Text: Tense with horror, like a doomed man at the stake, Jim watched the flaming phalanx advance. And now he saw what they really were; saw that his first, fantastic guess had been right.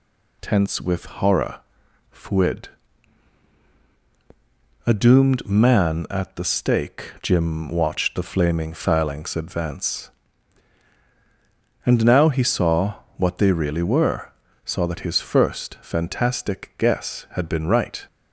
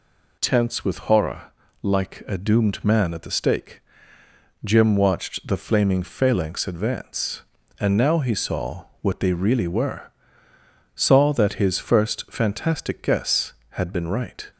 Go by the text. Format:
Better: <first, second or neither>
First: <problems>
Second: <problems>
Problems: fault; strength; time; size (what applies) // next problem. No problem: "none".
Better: second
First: says "fuid" for "like"; at 2.1 s // pauses between "saw" and "what"; slight; at 12.9 s; 0.25 s long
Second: pauses between "saw" and "what"; slight; at 8.8 s; 0.16 s long